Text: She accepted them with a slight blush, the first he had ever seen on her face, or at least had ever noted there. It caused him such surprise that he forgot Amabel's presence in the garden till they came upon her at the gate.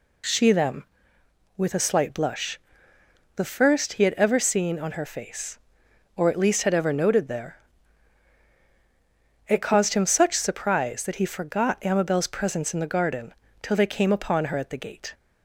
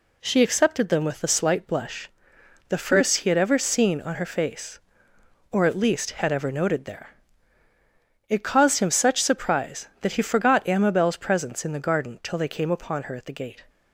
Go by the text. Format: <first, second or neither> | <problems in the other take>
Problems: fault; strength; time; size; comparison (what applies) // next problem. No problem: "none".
second | skips "accepted"; at 0.5 s // pauses between "garden" and "till"; slight; at 13.3 s; 0.26 s long